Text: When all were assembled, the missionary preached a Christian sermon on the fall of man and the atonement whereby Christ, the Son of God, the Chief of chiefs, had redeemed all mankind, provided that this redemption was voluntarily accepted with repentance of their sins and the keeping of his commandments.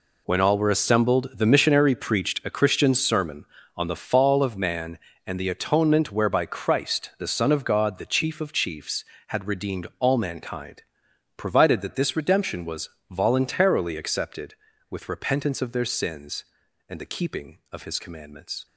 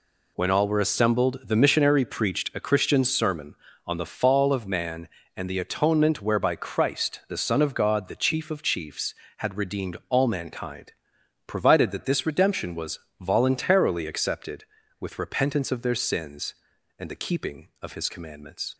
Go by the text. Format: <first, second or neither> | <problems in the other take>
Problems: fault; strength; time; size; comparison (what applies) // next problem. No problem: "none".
second | gets quieter; strong; throughout; 12 dB // pauses between "was" and "voluntarily"; slight; at 12.8 s; 0.22 s long; slight in the second